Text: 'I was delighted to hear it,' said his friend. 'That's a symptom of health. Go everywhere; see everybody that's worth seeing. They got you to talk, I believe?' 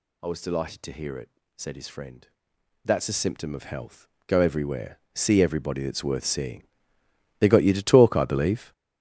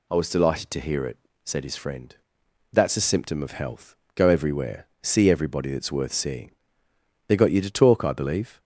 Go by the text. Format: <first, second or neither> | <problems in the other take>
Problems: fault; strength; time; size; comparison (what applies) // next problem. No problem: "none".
second | gets louder; strong; throughout; 11 dB